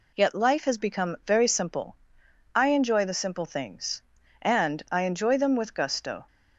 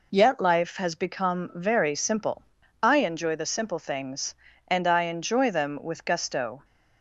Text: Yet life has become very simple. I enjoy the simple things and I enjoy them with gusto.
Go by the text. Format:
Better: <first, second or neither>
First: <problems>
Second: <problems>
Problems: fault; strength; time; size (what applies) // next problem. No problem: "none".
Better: neither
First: none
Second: none